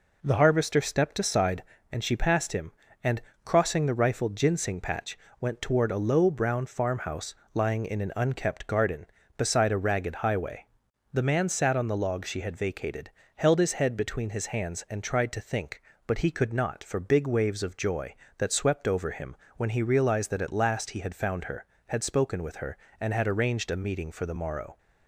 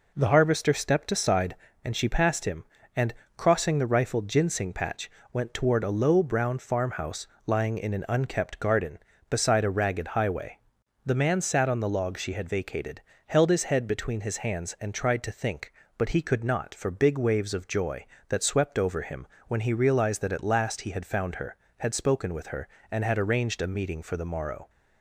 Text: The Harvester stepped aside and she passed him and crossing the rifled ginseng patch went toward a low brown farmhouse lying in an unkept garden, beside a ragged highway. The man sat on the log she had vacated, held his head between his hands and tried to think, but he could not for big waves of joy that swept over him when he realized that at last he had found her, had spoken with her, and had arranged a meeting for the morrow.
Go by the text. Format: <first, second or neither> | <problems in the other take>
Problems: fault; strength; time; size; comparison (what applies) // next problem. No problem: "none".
neither | pauses between "and" and "crossing"; slight; the same in both // pauses between "patch" and "went"; slight; the same in both // pauses between "farmhouse" and "lying"; slight; the same in both // pauses between "him" and "when"; slight; the same in both